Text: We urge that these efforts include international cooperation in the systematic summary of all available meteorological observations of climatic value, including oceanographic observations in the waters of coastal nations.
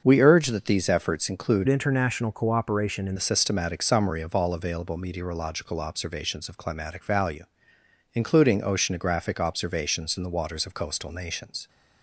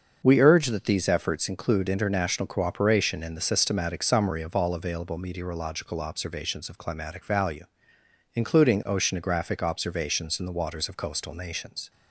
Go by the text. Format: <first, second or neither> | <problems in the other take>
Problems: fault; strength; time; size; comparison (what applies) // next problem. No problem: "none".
second | starts louder than the rest; until 1.0 s; 6.5 dB; also in the second // changes voice from "international" to "in"; from 1.6 to 3.1 s; 1.5 s long